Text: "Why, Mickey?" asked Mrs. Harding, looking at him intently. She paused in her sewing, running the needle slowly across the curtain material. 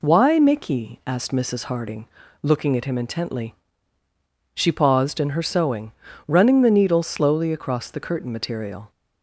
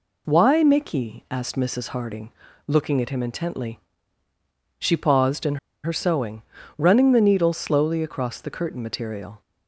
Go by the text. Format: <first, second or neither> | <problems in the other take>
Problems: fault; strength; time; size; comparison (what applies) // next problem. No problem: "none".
first | pauses between "in" and "her"; slight; at 5.5 s; 0.27 s long